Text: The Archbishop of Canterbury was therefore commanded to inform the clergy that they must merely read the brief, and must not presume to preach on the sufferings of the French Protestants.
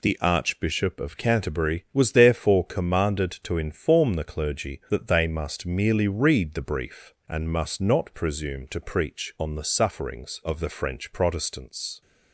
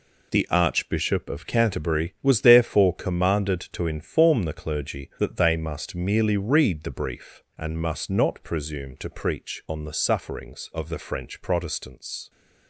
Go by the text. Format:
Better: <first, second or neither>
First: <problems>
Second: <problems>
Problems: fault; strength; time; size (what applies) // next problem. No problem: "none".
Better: first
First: none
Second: gets quieter; strong; throughout; 8 dB